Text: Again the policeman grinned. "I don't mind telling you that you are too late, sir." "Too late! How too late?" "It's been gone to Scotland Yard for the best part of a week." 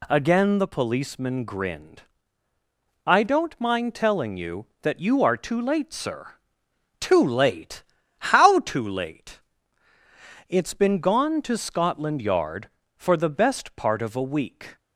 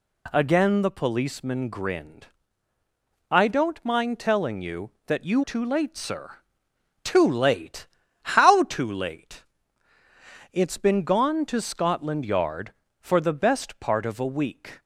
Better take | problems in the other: first | skips "are"; at 5.4 s

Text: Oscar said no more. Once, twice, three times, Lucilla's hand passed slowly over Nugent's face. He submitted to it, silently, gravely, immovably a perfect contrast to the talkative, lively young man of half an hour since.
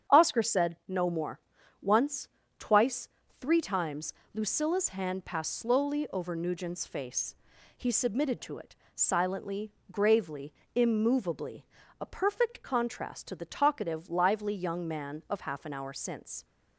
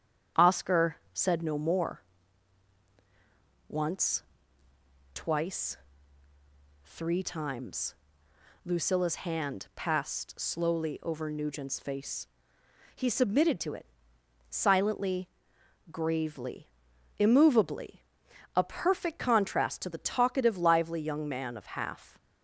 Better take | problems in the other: first | starts louder than the rest; strong; until 1.5 s; 8.5 dB; strong in the first // pauses between "Oscar" and "said"; slight; at 0.9 s; 0.16 s long // pauses between "immovably" and "a"; noticeable; at 17.9 s; 0.54 s long; slight in the first // stops before "an hour since"; at 22.1 s

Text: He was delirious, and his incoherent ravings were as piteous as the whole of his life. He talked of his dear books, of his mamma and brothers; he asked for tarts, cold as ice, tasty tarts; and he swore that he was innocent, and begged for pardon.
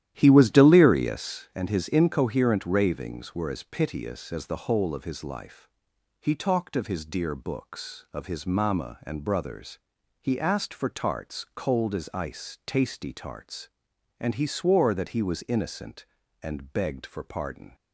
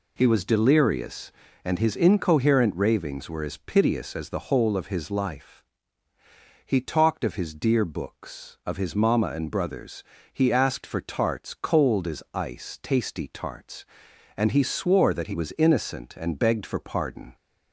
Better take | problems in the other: second | starts louder than the rest; strong; until 1.5 s; 12 dB

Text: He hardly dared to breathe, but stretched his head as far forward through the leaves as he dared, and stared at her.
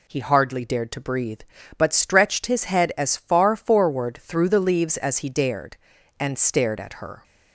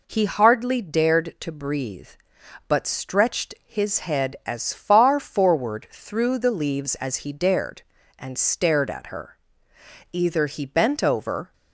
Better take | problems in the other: first | goes on to say "Either he bent over"; from 10.1 s on; 1.4 s long

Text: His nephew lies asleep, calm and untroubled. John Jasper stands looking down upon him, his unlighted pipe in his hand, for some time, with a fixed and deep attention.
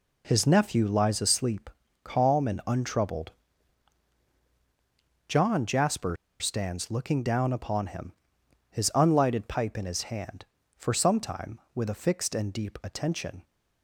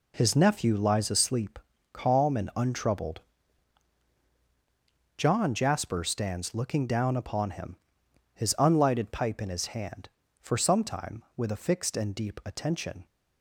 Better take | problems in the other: second | pauses between "Jasper" and "stands"; slight; at 6.1 s; 0.24 s long

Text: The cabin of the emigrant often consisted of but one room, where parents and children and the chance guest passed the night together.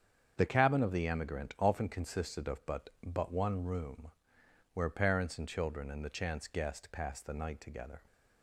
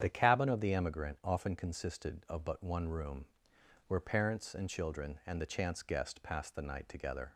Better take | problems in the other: second | starts louder than the rest; strong; until 1.3 s; 7.5 dB; strong in the second // says "but" twice; at 3.0 s

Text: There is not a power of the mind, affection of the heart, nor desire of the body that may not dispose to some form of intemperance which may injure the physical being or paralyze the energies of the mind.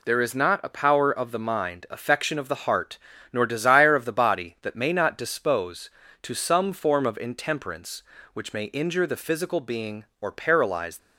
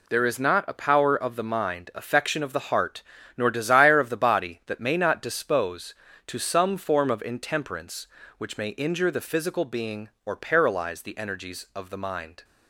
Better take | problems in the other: second | stops before "the energies of the mind"; at 10.9 s

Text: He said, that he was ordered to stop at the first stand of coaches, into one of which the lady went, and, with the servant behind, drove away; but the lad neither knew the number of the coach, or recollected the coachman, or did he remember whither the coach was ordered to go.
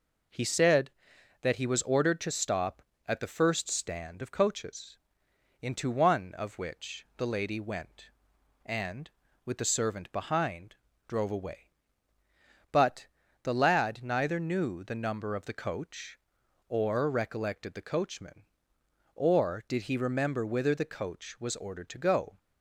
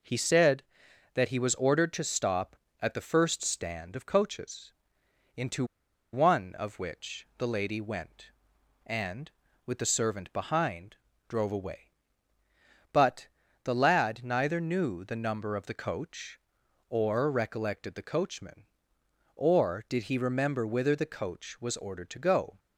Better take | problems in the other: first | pauses between "into" and "one"; noticeable; at 5.6 s; 0.48 s long // pauses between "but" and "the"; at 13.2 s; 0.38 s long; also in the first

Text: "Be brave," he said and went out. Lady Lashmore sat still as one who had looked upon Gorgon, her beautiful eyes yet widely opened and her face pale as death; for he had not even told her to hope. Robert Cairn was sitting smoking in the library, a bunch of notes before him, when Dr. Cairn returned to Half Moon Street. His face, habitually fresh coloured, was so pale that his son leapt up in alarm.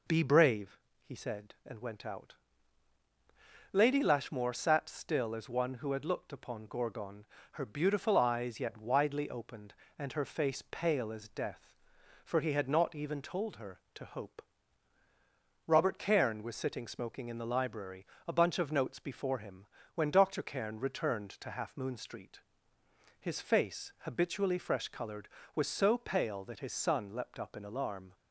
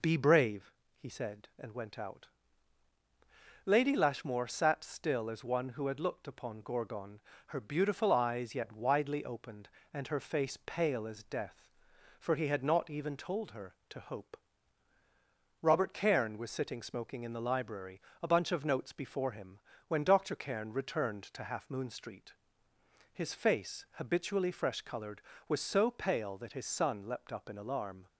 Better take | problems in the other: neither | none

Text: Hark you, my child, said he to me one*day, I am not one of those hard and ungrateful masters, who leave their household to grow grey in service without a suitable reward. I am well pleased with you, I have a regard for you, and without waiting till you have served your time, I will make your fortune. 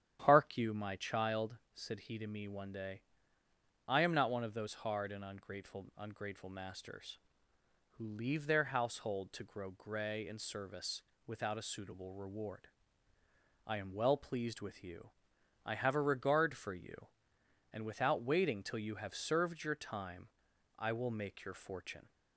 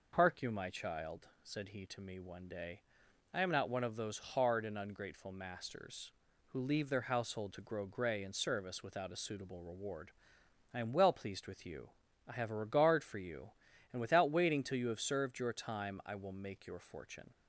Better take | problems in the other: second | starts louder than the rest; strong; until 1.2 s; 10 dB // says "ungrateful" twice; at 5.9 s // pauses between "service" and "without"; slight; at 11.0 s; 0.26 s long

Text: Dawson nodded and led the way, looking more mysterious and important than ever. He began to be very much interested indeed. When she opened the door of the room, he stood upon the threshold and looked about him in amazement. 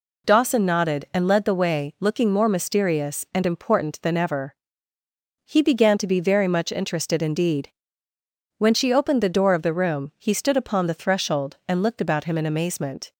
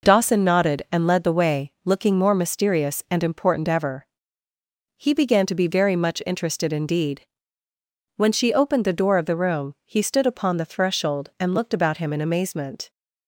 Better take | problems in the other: first | skips "than"; at 3.6 s

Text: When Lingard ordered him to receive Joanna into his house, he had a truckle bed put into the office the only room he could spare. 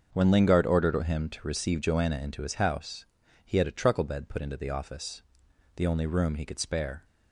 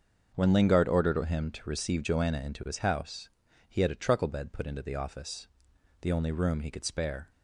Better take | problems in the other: neither | starts louder than the rest; the same in both // pauses between "office" and "the"; noticeable; the same in both

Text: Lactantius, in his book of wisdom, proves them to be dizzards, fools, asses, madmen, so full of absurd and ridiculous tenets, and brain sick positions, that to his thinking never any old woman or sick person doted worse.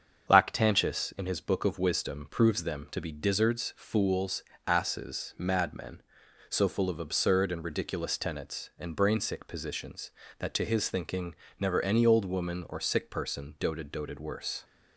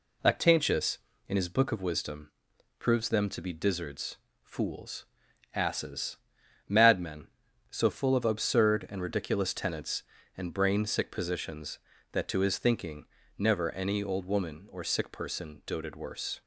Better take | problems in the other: second | starts louder than the rest; strong; until 1.3 s; 7 dB // pauses between "thinking" and "never"; slight; at 11.3 s; 0.26 s long; slight in the second // says "doted" twice; at 13.9 s

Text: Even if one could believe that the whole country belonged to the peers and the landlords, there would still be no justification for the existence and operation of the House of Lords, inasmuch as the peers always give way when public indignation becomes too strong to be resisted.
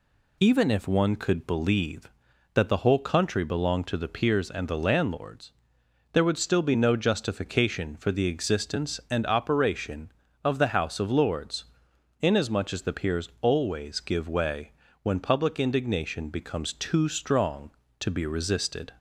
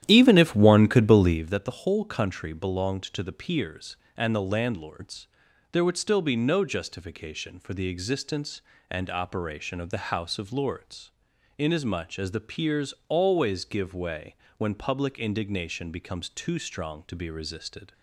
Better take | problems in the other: first | starts louder than the rest; strong; until 1.4 s; 11.5 dB // pauses between "way" and "when"; slight; at 14.3 s; 0.22 s long; slight in the first

